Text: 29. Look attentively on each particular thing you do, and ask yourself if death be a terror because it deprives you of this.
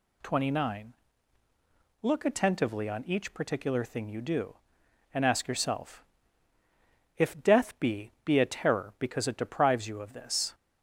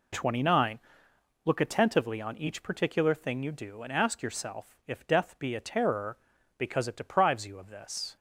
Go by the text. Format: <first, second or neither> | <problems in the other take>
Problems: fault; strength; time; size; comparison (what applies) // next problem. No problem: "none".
second | pauses between "yourself" and "if"; at 6.0 s; 1.1 s long // says "be" twice; at 8.2 s